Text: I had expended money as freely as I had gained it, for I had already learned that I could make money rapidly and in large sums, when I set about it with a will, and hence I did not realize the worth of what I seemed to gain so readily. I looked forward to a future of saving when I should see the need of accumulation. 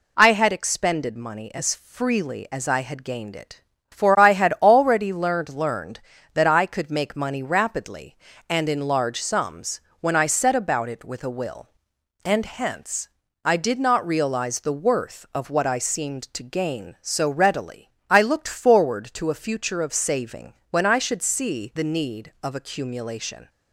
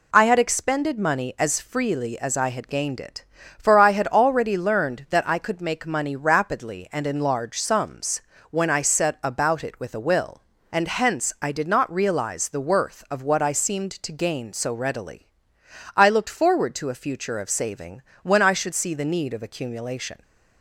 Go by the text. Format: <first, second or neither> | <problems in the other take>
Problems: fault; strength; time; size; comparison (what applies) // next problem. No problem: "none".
second | says "learned" twice; at 5.4 s // pauses between "hence" and "I"; slight; at 13.0 s; 0.36 s long // pauses between "saving" and "when"; slight; at 20.5 s; 0.18 s long; slight in the second